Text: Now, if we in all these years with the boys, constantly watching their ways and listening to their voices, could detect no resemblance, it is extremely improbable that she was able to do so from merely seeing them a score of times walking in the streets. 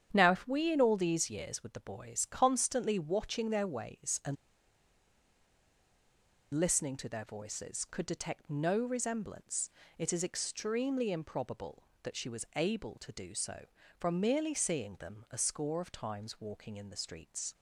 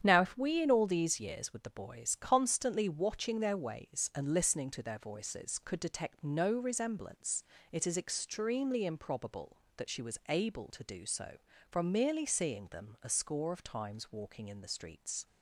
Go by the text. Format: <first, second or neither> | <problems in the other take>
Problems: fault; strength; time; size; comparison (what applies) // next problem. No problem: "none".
second | starts louder than the rest; strong; until 1.1 s; 9 dB; strong in the second // pauses between "and" and "listening"; strong; at 4.3 s; 2.1 s long